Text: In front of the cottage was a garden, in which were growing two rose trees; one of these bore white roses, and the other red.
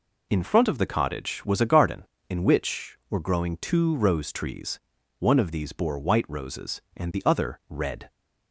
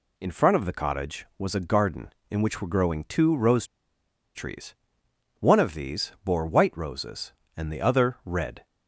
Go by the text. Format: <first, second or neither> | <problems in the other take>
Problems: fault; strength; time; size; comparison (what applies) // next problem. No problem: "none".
first | pauses between "rose" and "trees"; noticeable; at 3.6 s; 0.68 s long